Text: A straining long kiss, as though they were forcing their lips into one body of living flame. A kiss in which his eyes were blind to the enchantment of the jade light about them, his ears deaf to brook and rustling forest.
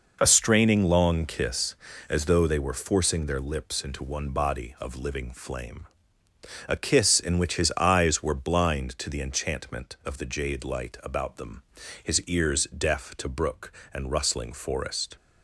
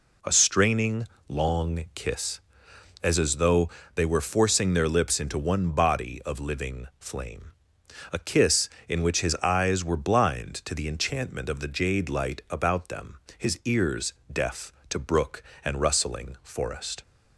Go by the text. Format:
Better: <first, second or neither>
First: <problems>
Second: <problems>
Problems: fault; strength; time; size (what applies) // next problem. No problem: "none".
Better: first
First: none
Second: pauses between "straining" and "long"; slight; at 1.0 s; 0.24 s long // says "as" twice; at 3.1 s // pauses between "though" and "they"; slight; at 3.6 s; 0.24 s long // pauses between "ears" and "deaf"; slight; at 14.1 s; 0.18 s long